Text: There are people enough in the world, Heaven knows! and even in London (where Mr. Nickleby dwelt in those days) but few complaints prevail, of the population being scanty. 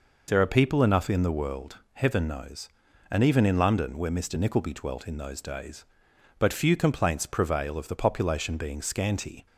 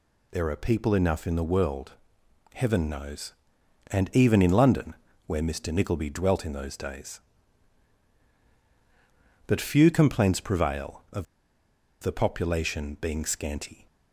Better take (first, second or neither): first